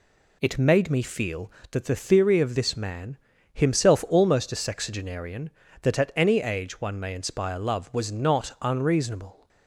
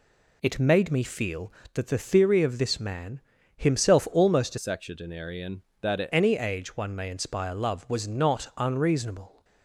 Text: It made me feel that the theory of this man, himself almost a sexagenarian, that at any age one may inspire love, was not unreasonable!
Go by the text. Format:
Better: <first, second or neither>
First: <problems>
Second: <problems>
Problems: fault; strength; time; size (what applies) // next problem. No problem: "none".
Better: first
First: none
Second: changes voice from "sexagenarian" to "at"; from 4.5 to 6.0 s; 1.5 s long